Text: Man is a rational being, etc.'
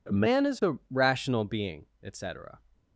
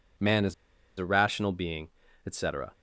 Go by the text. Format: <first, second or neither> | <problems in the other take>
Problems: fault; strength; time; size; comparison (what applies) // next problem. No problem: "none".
first | pauses between "is" and "a"; at 0.5 s; 0.43 s long